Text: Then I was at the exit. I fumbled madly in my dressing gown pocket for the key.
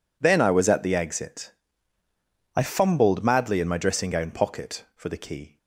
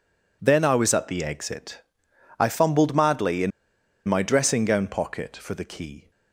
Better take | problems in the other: first | pauses between "in" and "my"; noticeable; at 3.5 s; 0.57 s long

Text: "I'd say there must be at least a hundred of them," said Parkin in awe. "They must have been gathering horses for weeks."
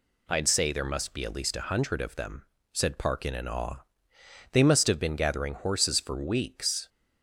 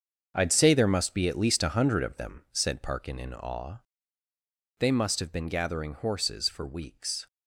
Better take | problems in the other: first | gets quieter; strong; throughout; 11 dB

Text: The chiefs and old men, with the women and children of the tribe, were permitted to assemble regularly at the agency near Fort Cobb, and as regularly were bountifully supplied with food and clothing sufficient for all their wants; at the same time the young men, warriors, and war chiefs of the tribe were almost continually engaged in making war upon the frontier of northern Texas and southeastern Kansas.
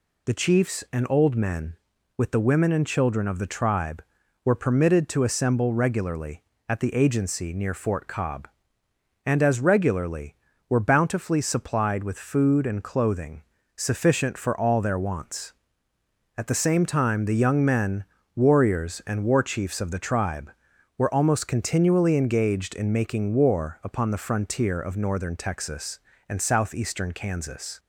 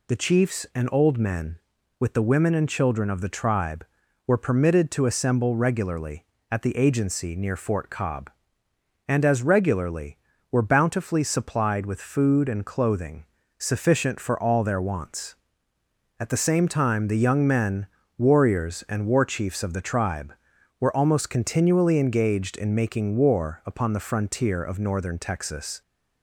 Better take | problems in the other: first | pauses between "clothing" and "sufficient"; slight; at 13.2 s; 0.32 s long; slight in the first // stops before "and southeastern Kansas"; at 25.8 s

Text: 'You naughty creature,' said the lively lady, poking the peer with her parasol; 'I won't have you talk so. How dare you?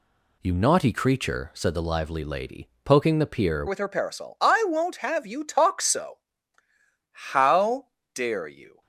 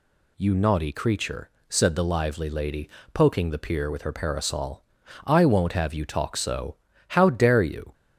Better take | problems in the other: second | changes voice at "with"; from 3.6 s on; 5.2 s long // pauses between "How" and "dare"; slight; at 7.9 s; 0.24 s long

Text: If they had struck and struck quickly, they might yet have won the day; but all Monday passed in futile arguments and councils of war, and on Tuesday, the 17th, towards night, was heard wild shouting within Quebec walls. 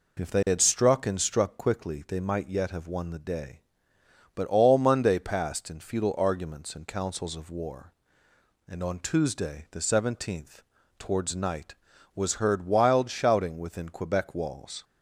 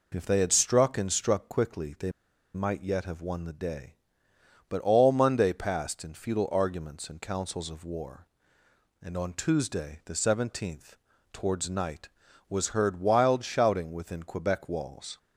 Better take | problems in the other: first | pauses between "they" and "might"; at 2.1 s; 0.43 s long

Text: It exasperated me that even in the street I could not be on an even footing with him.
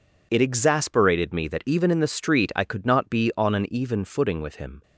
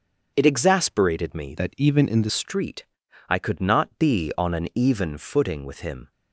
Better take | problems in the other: first | starts louder than the rest; until 1.3 s; 6 dB // changes voice from "that" to "the"; from 1.5 to 2.3 s; 0.8 s long // pauses between "street" and "I"; at 2.8 s; 0.44 s long

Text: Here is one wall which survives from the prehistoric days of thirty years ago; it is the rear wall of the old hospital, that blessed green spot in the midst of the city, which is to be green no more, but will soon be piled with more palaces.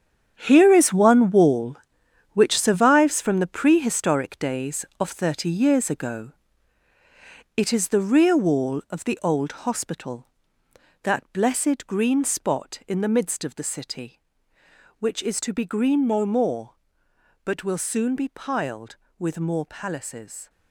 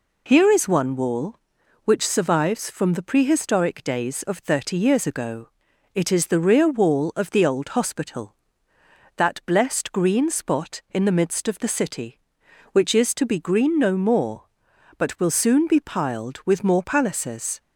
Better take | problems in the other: second | gets quieter; strong; throughout; 11.5 dB

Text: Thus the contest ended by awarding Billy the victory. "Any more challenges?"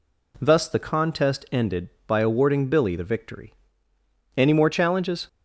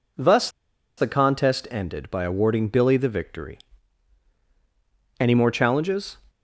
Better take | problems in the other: first | pauses between "Thus" and "the"; noticeable; at 0.4 s; 0.49 s long

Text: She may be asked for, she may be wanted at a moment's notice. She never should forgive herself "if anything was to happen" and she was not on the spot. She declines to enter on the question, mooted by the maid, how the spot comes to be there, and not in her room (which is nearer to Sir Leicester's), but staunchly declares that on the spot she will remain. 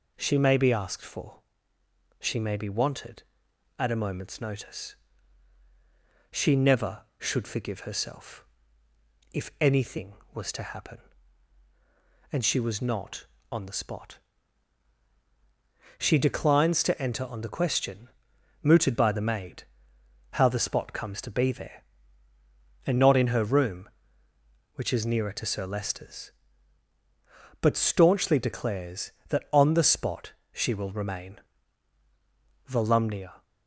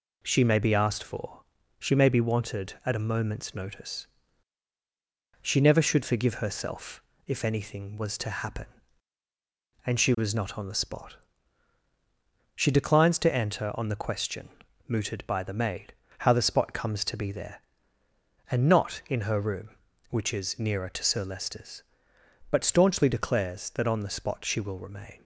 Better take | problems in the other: second | pauses between "herself" and "if"; noticeable; at 8.4 s; 0.86 s long; slight in the second // pauses between "spot" and "she"; slight; at 30.3 s; 0.20 s long // goes on to say "Volumnia"; noticeable; from 32.6 s on; 0.74 s long

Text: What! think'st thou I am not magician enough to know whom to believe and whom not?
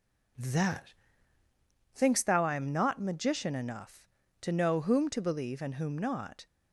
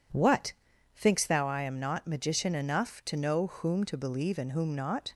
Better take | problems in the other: second | says "That" for "What"; at 0.3 s

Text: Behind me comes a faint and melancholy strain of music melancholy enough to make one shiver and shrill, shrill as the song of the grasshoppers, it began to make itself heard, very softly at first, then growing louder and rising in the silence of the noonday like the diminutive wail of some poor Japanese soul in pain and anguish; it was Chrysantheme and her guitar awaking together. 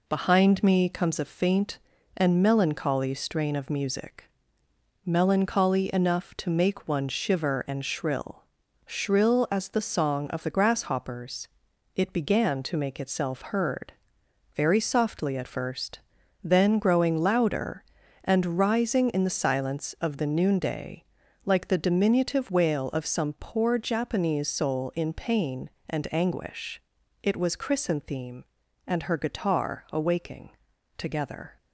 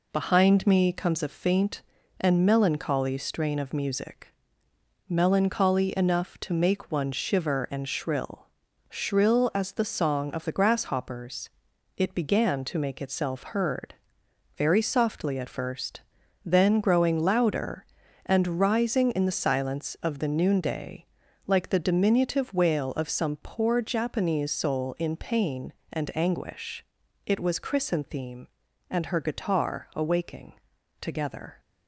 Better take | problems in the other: neither | pauses between "music" and "melancholy"; noticeable; the same in both // pauses between "noonday" and "like"; the same in both // pauses between "awaking" and "together"; the same in both

